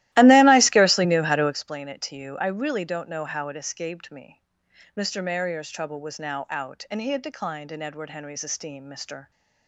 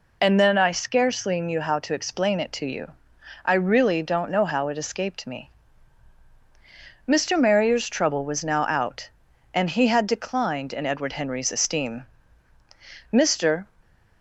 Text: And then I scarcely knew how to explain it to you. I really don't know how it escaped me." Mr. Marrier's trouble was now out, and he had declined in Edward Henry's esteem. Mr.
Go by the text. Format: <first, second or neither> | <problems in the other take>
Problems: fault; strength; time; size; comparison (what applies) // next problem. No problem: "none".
second | starts louder than the rest; strong; until 1.6 s; 16 dB